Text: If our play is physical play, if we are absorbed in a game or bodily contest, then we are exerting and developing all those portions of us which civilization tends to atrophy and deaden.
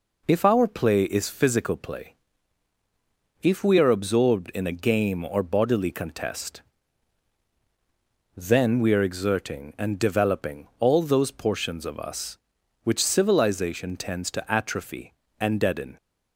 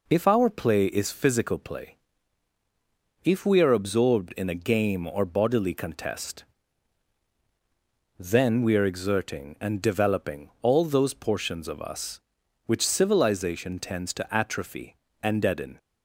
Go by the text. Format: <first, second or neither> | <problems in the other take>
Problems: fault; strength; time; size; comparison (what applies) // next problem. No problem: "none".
neither | none